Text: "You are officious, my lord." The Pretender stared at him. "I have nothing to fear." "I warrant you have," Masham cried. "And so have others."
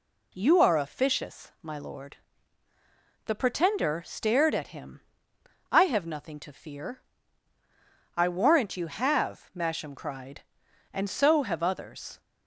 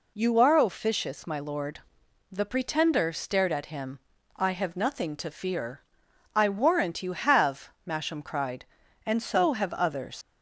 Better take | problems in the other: first | leaves "others" unfinished; at 10.2 s; 100 ms

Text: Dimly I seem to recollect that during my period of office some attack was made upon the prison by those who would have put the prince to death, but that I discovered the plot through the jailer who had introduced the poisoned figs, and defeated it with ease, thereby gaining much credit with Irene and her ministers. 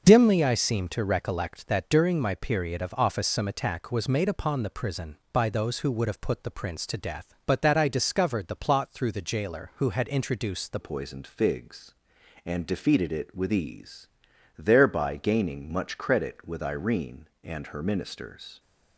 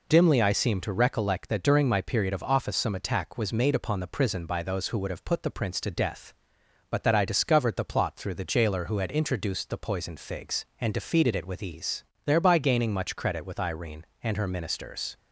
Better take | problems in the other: second | starts louder than the rest; until 1.0 s; 6 dB // changes voice at "poisoned"; from 10.8 s on; 7.7 s long

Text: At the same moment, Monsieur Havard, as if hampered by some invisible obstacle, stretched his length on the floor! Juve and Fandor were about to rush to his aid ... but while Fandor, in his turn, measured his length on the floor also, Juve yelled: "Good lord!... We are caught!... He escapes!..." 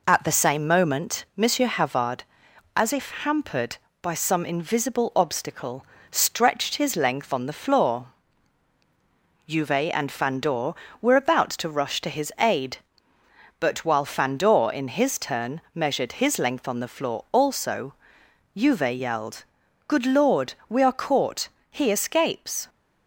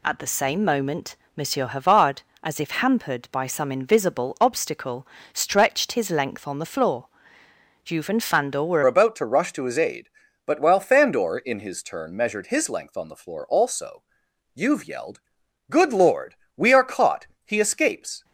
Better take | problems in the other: first | changes voice at "about"; from 8.8 s on; 9.4 s long

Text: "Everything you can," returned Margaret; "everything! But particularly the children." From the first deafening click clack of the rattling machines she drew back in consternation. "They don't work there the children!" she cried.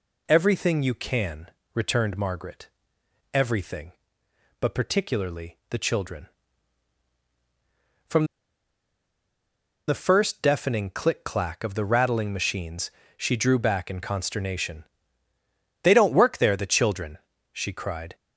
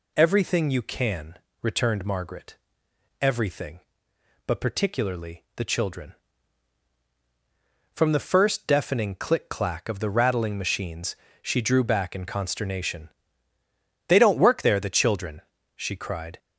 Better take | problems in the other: second | pauses between "From" and "the"; strong; at 8.2 s; 1.6 s long // pauses between "machines" and "she"; slight; at 12.9 s; 0.26 s long; slight in the second

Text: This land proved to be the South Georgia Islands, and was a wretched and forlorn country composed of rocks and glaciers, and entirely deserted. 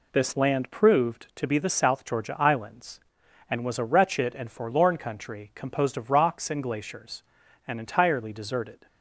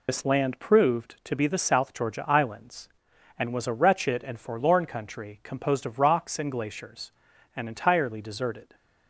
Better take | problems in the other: first | loses the start of "This"; at 0.0 s; 80 ms

